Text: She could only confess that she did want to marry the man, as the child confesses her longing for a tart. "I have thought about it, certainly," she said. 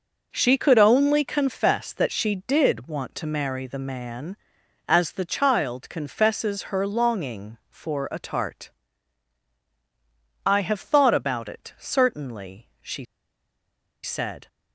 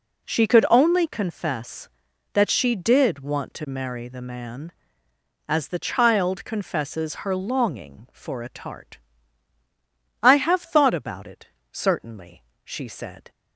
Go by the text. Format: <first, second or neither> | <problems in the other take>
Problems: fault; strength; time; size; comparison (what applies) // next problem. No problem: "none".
second | pauses between "she" and "said"; at 13.0 s; 0.99 s long